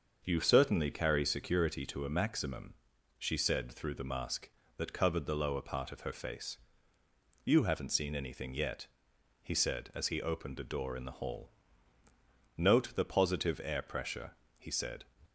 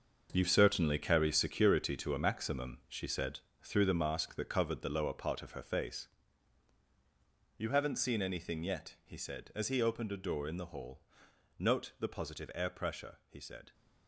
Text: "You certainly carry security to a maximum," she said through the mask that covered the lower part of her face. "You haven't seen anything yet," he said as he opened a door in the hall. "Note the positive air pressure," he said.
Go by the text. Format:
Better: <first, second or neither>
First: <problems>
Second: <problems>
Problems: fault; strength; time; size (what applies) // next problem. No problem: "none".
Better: first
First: starts louder than the rest; until 1.2 s; 6.5 dB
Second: gets quieter; strong; throughout; 10.5 dB // starts louder than the rest; until 1.3 s; 6 dB // pauses between "said" and "through"; slight; at 3.4 s; 0.22 s long